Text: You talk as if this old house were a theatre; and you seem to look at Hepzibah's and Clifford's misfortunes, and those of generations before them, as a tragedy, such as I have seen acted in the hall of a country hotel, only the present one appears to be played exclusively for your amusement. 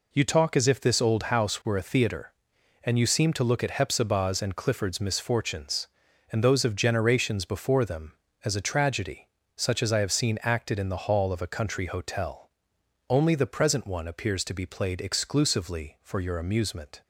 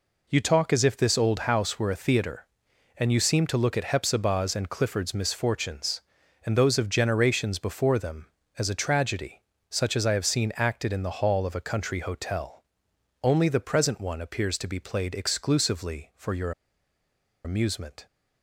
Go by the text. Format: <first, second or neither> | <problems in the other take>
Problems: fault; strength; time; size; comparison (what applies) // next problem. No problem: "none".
first | pauses between "your" and "amusement"; noticeable; at 16.5 s; 0.93 s long